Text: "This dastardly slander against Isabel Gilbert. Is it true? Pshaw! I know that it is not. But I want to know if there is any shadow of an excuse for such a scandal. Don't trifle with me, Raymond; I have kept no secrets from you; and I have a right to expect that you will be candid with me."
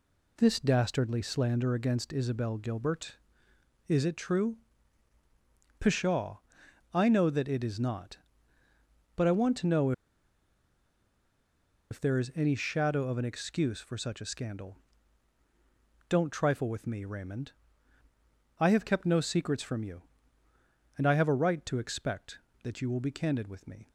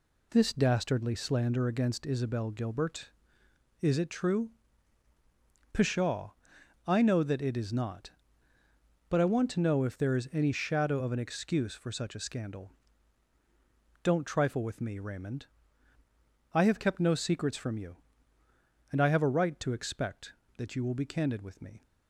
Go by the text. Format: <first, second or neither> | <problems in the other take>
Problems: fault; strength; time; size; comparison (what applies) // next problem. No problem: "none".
second | pauses between "know" and "if"; strong; at 9.9 s; 1.9 s long